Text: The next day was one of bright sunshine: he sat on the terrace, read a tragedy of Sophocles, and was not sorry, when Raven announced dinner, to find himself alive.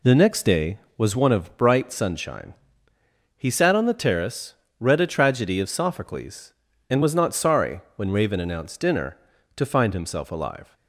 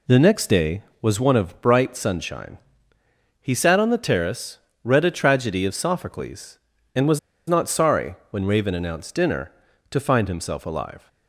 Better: first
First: none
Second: pauses between "was" and "not"; slight; at 7.1 s; 0.28 s long

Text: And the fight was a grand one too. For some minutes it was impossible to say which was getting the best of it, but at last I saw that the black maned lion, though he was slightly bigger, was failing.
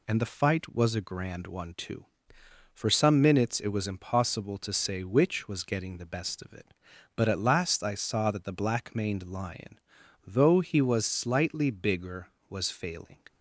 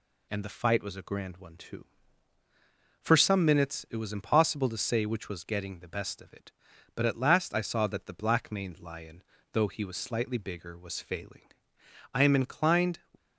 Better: first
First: none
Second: goes on to say "I am inclined"; noticeable; from 12.1 s on; 0.86 s long

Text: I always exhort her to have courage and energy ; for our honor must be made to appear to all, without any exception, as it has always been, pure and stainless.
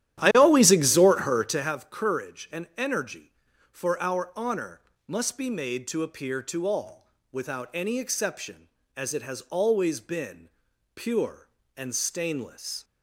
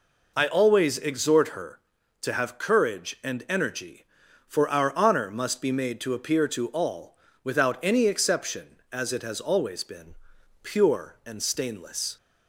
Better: second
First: starts louder than the rest; strong; until 1.8 s; 11.5 dB // pauses between "honor" and "must"; slight; at 4.7 s; 0.28 s long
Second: none

